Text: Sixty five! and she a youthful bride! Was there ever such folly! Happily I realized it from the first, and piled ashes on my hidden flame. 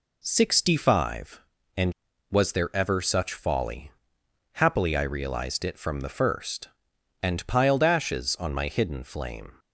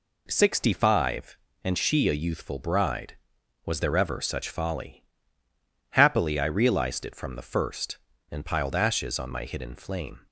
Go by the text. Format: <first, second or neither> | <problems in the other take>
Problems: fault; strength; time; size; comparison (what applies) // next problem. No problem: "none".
second | skips "she a youthful bride"; at 2.1 s